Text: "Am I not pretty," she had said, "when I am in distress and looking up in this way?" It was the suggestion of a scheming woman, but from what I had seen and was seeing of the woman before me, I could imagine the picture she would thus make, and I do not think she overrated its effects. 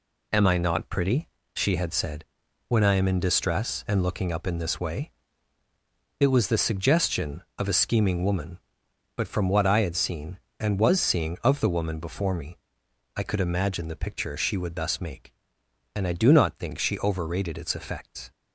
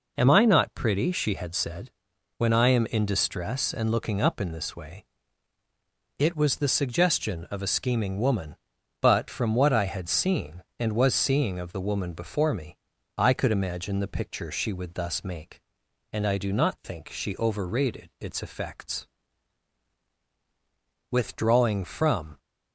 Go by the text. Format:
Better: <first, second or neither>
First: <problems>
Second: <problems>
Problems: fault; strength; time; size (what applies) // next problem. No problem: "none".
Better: first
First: none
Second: goes on to say "Withdrawing from"; noticeable; from 21.0 s on; 1.2 s long